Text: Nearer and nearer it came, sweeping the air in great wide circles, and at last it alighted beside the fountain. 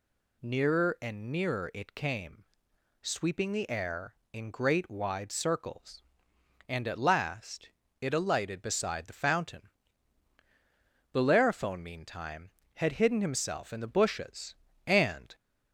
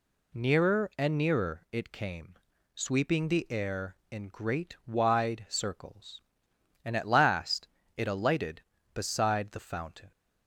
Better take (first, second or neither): second